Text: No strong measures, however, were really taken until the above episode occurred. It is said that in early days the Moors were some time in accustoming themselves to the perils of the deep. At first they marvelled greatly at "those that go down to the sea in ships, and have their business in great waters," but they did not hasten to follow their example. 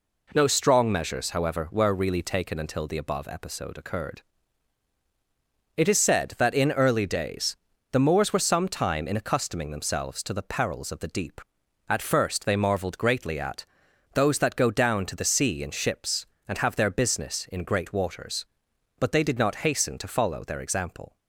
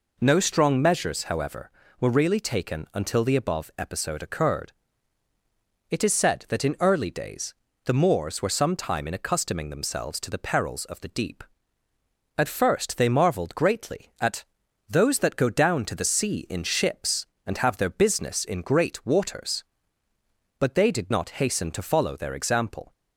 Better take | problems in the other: neither | pauses between "days" and "the"; slight; the same in both // pauses between "at" and "those"; noticeable; the same in both

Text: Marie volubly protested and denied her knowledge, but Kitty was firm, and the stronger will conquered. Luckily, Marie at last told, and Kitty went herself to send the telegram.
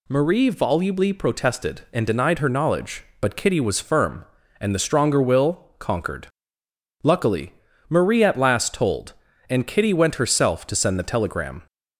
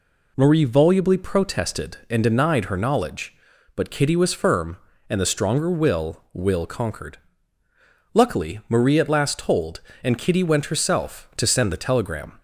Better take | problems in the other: first | says "will" twice; at 6.3 s

